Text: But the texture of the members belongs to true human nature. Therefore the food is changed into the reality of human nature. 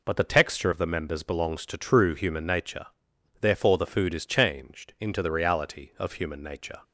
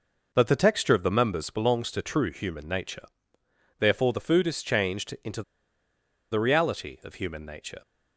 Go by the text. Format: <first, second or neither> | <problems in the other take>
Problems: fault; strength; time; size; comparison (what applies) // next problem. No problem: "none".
first | pauses between "into" and "the"; noticeable; at 5.4 s; 0.89 s long